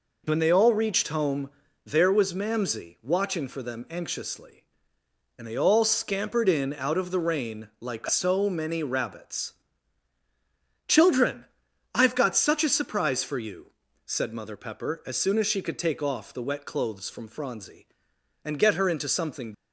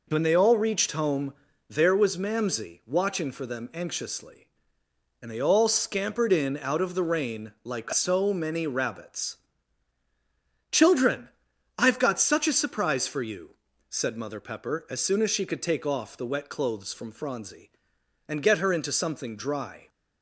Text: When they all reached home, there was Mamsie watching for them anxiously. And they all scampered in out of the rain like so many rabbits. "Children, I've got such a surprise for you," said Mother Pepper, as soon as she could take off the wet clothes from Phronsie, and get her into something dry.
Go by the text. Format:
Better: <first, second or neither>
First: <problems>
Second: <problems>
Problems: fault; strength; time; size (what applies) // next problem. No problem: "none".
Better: second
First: stops before "dry"; at 19.5 s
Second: none